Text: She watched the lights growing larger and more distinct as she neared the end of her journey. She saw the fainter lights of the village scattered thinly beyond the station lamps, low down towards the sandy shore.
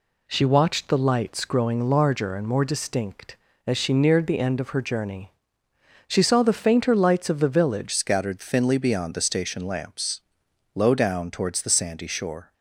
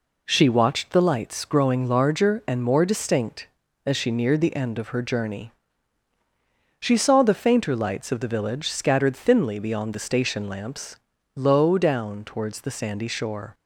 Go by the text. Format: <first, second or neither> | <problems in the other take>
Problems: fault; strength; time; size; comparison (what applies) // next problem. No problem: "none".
second | changes voice at "scattered"; from 7.9 s on; 4.6 s long